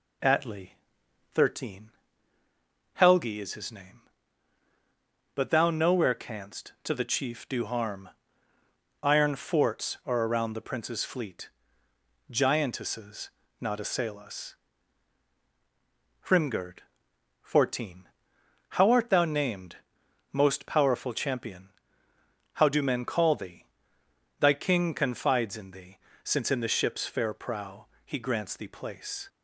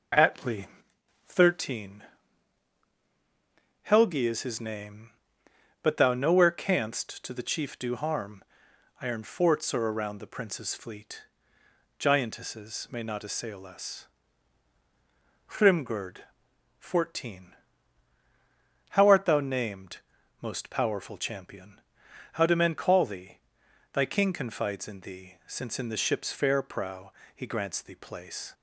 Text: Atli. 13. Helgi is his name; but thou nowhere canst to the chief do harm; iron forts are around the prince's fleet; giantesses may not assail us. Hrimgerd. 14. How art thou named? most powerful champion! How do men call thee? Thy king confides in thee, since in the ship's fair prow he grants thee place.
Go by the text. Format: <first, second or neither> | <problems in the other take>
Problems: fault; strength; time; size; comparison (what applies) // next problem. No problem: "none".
second | skips "may"; at 13.4 s // pauses between "prow" and "he"; slight; at 27.8 s; 0.18 s long; slight in the second